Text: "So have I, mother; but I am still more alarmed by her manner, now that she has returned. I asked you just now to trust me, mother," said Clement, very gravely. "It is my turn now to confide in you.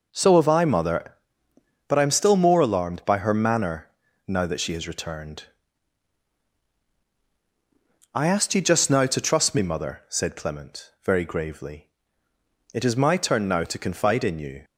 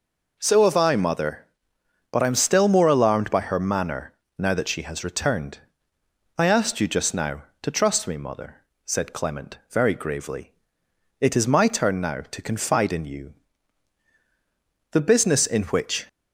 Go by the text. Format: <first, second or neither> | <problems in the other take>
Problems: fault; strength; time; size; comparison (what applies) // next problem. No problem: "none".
first | goes on to say "The business in which"; noticeable; from 14.9 s on; 1.1 s long